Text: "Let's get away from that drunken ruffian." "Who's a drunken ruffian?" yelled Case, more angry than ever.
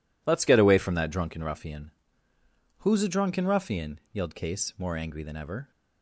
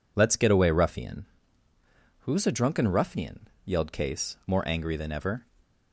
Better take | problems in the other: first | skips "from that drunken"; at 0.7 s

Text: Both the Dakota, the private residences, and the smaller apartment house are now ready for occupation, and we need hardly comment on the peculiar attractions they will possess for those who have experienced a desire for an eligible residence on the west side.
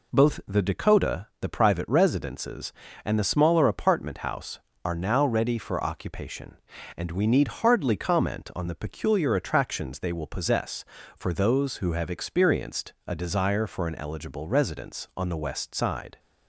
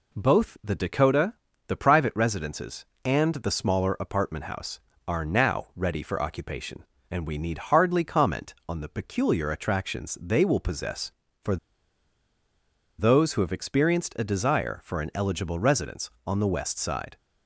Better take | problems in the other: first | pauses between "for" and "those"; strong; at 11.5 s; 1.4 s long

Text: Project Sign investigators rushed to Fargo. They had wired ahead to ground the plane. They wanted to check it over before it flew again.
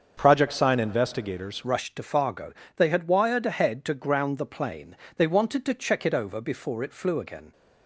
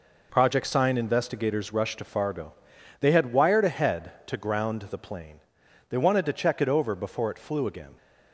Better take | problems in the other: second | starts louder than the rest; until 1.1 s; 6.5 dB // changes voice at "rushed"; from 1.6 s on; 5.9 s long

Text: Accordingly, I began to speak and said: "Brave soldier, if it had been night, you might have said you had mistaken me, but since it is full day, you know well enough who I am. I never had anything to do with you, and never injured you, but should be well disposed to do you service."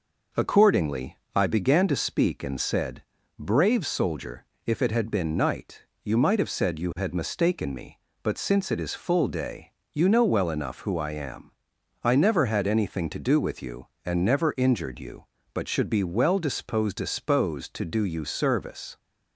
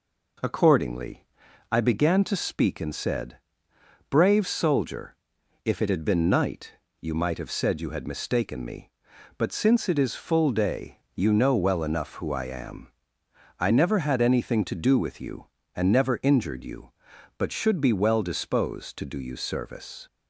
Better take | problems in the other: second | says "disposed" twice; at 16.9 s

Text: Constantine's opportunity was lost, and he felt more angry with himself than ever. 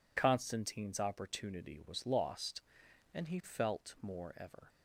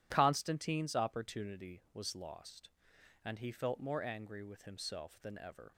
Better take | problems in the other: second | skips "angry with himself than"; at 4.3 s

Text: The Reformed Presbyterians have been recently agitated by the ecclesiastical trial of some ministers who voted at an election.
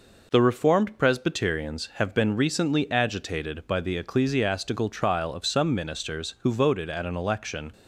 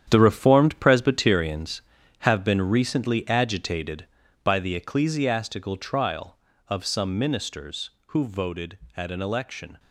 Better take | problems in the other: first | gets quieter; strong; throughout; 10 dB

